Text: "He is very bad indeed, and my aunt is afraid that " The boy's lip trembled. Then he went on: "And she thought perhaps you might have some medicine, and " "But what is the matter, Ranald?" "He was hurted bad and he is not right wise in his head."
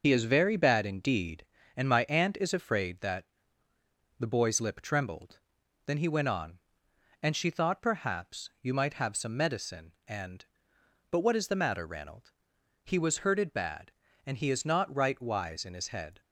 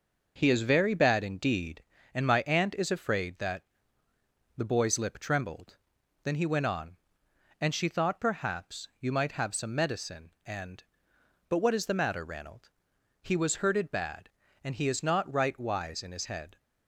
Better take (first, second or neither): second